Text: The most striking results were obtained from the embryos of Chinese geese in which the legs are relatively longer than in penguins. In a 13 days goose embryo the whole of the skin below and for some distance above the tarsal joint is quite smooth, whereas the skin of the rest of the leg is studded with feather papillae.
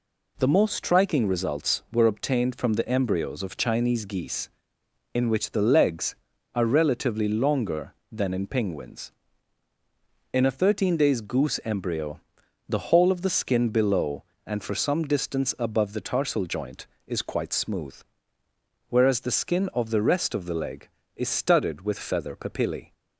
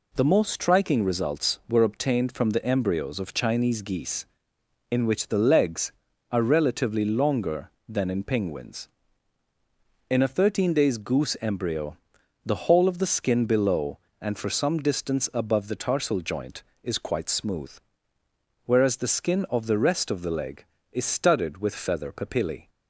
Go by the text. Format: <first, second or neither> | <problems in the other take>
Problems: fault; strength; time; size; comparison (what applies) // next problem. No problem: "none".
neither | pauses between "embryo" and "the"; noticeable; the same in both